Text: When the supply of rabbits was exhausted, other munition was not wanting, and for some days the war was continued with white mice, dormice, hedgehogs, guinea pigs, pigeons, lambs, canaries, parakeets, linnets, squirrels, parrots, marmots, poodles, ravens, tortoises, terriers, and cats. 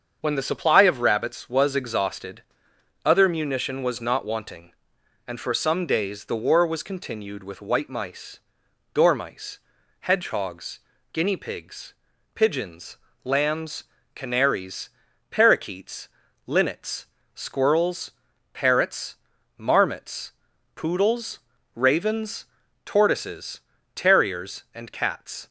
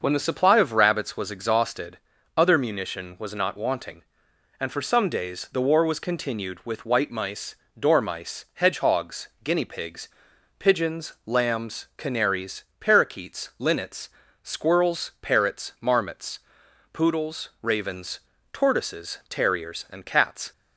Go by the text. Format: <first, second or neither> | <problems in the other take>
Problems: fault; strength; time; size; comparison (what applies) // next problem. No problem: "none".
neither | starts louder than the rest; the same in both